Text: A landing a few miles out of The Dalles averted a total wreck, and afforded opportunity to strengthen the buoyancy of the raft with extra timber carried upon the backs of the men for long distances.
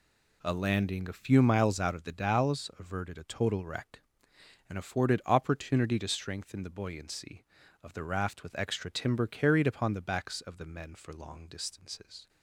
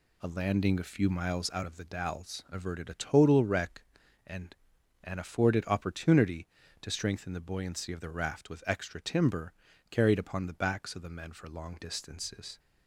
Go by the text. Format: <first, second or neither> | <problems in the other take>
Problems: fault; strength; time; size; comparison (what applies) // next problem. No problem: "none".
first | says "and" twice; at 5.0 s // pauses between "timber" and "carried"; at 9.5 s; 0.38 s long